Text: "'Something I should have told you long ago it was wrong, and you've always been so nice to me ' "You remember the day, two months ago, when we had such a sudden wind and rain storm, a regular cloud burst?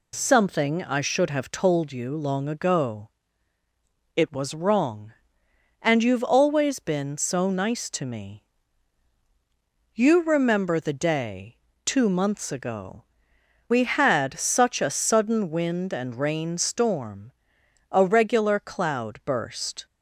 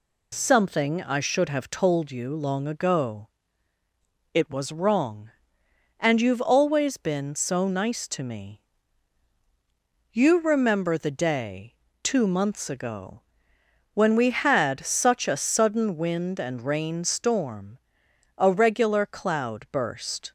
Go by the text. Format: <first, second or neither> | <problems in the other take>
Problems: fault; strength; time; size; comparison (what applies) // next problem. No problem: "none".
second | pauses between "ago" and "it"; at 3.0 s; 1.0 s long; also in the second // skips "when"; at 13.3 s